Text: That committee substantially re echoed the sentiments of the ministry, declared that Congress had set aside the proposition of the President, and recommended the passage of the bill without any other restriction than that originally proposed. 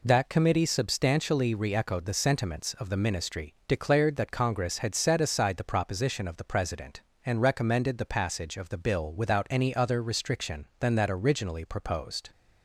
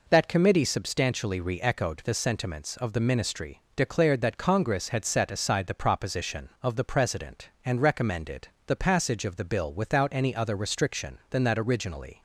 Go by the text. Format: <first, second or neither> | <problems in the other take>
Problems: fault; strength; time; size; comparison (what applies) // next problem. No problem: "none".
first | pauses between "recommended" and "the"; slight; at 8.4 s; 0.20 s long // stops before "proposed"; at 12.1 s